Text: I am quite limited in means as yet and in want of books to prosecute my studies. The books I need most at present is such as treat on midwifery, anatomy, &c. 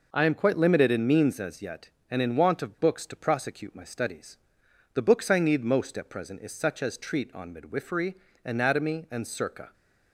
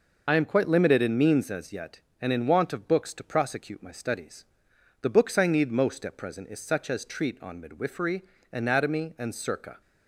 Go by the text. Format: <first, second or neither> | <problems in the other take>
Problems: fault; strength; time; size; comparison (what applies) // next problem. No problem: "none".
first | loses the start of "I"; at 0.2 s; 45 ms